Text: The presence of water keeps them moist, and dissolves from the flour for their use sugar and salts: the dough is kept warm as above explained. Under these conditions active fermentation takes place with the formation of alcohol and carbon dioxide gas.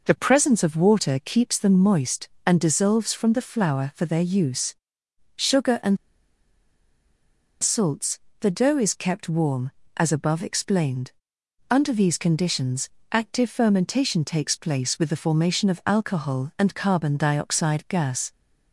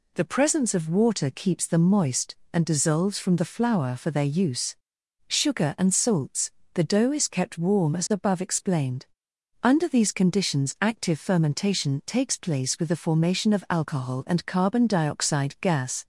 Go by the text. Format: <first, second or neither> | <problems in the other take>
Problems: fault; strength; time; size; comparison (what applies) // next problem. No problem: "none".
second | pauses between "use" and "sugar"; noticeable; at 4.7 s; 0.62 s long; noticeable in the second // pauses between "and" and "salts"; strong; at 5.9 s; 1.6 s long // pauses between "conditions" and "active"; slight; at 12.8 s; 0.24 s long